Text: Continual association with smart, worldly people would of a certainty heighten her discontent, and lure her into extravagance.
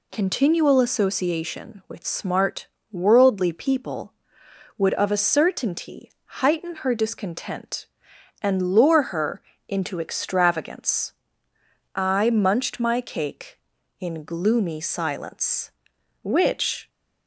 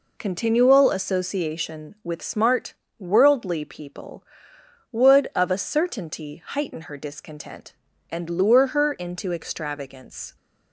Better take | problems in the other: second | pauses between "certainty" and "heighten"; slight; at 6.1 s; 0.16 s long // pauses between "her" and "into"; slight; at 9.4 s; 0.26 s long // goes on to say "I munched my cake in gloomy silence which"; strong; from 11.9 s on; 4.9 s long

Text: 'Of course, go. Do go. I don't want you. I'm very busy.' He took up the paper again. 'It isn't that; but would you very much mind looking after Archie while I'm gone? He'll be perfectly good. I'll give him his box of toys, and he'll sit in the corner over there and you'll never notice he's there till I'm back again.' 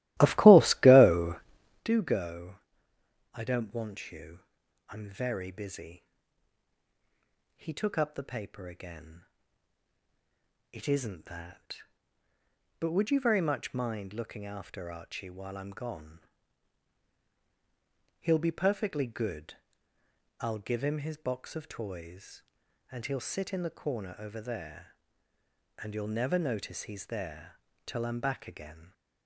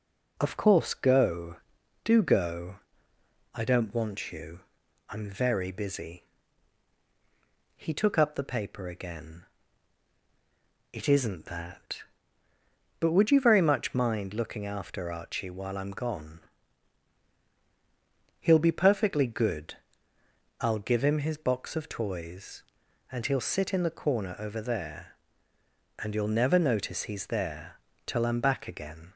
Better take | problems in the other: second | starts louder than the rest; strong; until 1.9 s; 15.5 dB // pauses between "there" and "till"; slight; at 27.5 s; 0.28 s long; slight in the second

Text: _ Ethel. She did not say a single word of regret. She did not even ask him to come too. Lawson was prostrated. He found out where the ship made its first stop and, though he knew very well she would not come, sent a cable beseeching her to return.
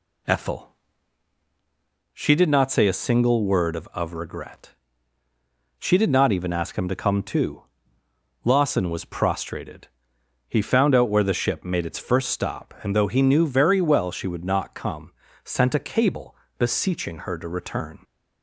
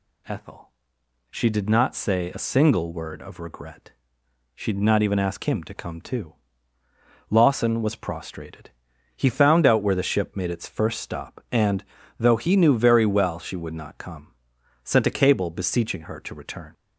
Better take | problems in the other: second | says "of" twice; at 3.9 s // pauses between "cable" and "beseeching"; slight; at 16.3 s; 0.24 s long

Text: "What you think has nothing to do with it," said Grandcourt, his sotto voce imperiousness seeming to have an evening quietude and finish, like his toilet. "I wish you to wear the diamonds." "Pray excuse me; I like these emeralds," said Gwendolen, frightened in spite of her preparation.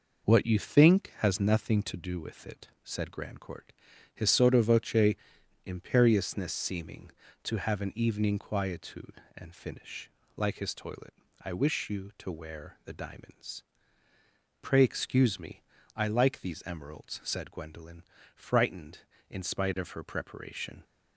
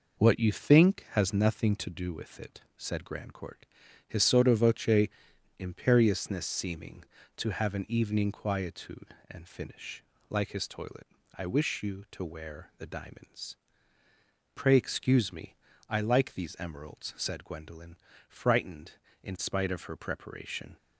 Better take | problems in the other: neither | pauses between "voce" and "imperiousness"; noticeable; the same in both

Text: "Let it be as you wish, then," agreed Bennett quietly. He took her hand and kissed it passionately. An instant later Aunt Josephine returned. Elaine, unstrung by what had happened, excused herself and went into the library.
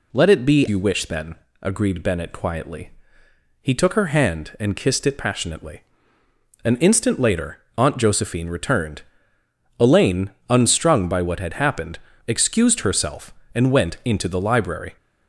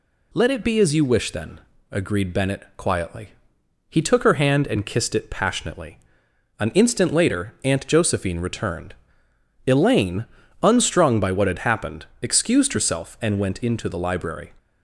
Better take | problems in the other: second | skips "as"; at 0.6 s // pauses between "later" and "Aunt"; slight; at 7.5 s; 0.20 s long

